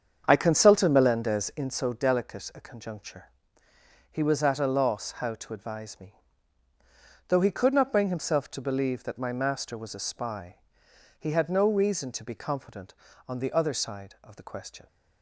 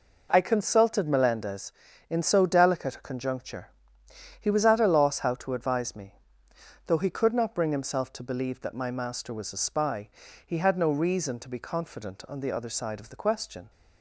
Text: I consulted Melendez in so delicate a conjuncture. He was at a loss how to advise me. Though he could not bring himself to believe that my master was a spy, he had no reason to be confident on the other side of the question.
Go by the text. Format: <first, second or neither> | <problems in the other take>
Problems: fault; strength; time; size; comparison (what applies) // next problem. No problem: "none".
second | starts louder than the rest; strong; until 1.7 s; 7.5 dB